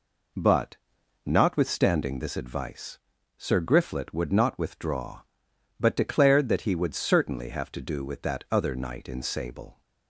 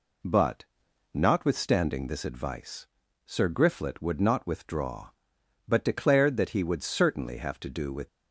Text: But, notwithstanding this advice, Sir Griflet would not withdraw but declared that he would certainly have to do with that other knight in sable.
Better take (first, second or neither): first